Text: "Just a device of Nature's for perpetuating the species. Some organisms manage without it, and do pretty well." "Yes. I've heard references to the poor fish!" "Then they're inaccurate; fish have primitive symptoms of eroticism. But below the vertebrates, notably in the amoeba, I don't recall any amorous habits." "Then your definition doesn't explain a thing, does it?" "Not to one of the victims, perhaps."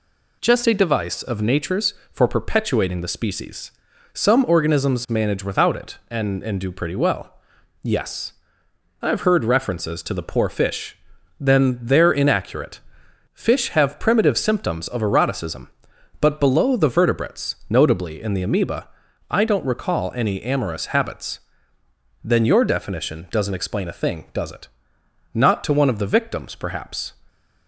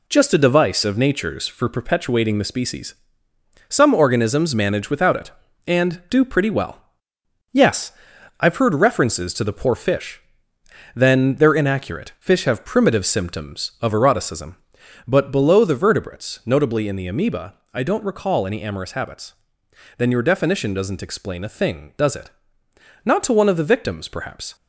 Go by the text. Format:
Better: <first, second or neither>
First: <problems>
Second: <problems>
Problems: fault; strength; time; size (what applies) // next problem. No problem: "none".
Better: second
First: says "and" twice; at 6.4 s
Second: none